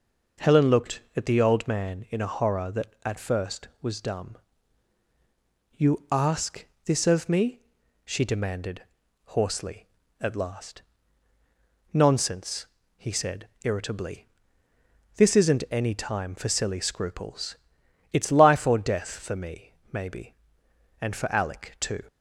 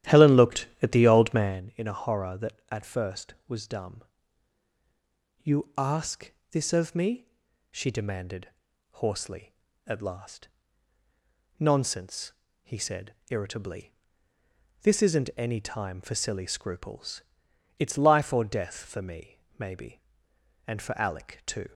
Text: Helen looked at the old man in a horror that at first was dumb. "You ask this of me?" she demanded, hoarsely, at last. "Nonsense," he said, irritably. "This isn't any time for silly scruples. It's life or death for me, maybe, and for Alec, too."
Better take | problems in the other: first | starts louder than the rest; strong; until 1.6 s; 12.5 dB // pauses between "ask" and "this"; slight; at 6.3 s; 0.20 s long; slight in the first

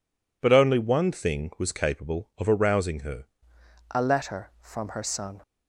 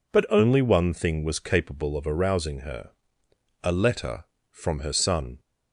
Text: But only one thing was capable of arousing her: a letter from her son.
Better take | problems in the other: second | changes voice at "a"; from 3.9 s on; 1.5 s long

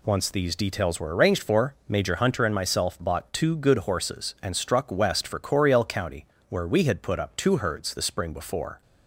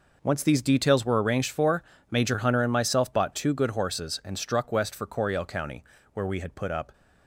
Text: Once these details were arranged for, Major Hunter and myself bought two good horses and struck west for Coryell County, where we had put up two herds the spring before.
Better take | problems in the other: first | stops before "two herds the spring before"; at 6.9 s

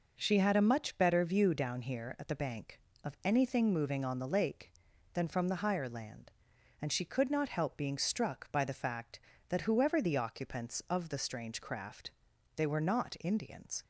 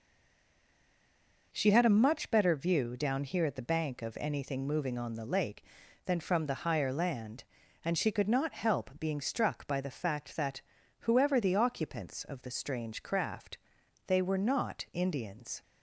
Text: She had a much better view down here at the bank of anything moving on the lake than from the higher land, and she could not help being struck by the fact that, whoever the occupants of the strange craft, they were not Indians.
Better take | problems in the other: first | stays silent before the first word; noticeable; until 1.5 s; 1.5 s long

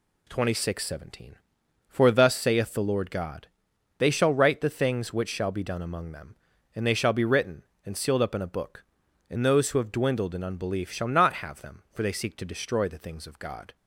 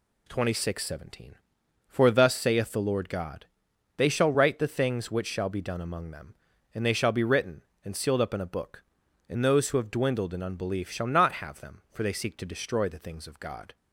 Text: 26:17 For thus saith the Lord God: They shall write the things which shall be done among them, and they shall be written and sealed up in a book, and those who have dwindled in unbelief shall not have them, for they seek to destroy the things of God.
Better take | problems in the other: neither | none

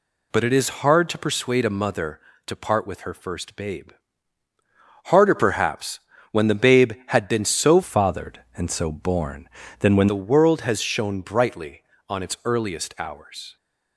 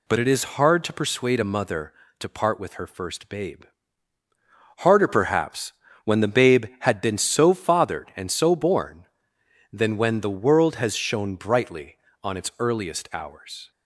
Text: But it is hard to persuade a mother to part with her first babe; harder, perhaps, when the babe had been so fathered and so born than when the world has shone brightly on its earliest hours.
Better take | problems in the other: second | changes voice from "fathered" to "when"; from 7.8 to 10.0 s; 2.2 s long

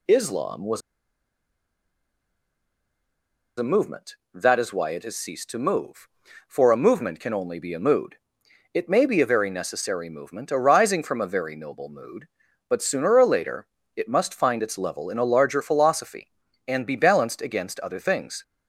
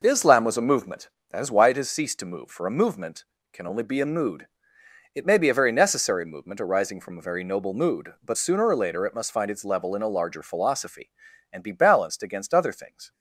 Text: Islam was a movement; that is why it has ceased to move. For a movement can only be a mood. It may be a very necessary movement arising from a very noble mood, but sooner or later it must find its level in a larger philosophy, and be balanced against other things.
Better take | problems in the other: second | pauses between "was" and "a"; strong; at 0.8 s; 2.7 s long // pauses between "later" and "it"; slight; at 13.6 s; 0.26 s long

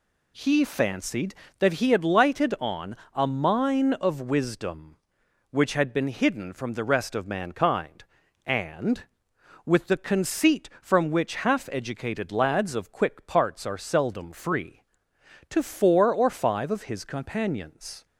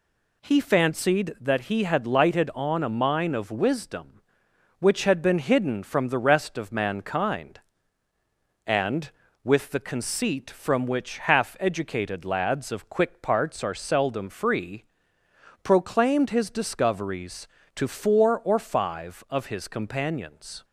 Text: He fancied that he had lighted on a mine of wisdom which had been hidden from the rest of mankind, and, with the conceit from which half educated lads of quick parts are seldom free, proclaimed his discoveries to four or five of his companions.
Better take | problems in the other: second | pauses between "on" and "a"; slight; at 2.9 s; 0.16 s long // skips "proclaimed his discoveries"; at 15.1 s

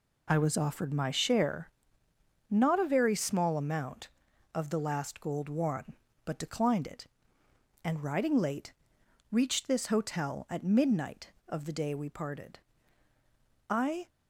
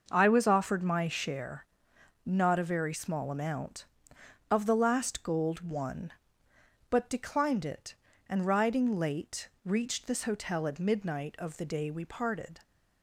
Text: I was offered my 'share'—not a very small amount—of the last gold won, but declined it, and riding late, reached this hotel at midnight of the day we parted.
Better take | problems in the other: second | goes on to say "I"; slight; from 13.7 s on; 0.38 s long

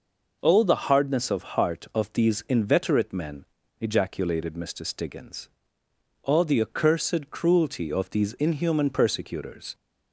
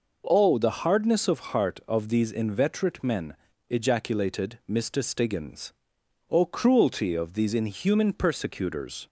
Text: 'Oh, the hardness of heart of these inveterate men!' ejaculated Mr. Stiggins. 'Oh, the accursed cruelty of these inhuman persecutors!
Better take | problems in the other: first | skips "the accursed"; at 6.4 s

